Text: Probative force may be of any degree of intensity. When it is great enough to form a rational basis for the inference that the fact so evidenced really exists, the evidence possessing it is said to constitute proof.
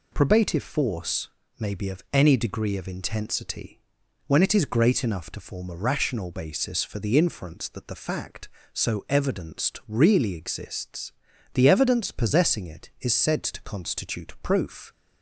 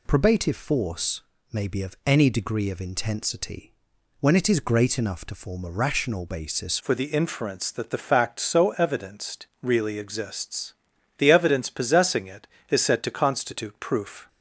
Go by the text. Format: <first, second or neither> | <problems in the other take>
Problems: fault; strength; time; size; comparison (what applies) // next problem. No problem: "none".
first | pauses between "force" and "may"; slight; at 1.2 s; 0.30 s long; slight in the first // changes voice at "for"; from 6.8 s on; 7.4 s long // pauses between "evidenced" and "really"; slight; at 9.4 s; 0.16 s long